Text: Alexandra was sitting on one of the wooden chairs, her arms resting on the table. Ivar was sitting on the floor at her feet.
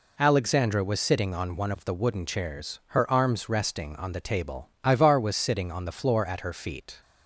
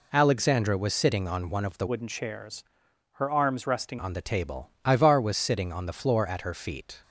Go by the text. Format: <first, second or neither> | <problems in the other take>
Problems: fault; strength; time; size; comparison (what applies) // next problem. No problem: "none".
first | changes voice from "wooden" to "resting"; from 1.8 to 3.9 s; 2.1 s long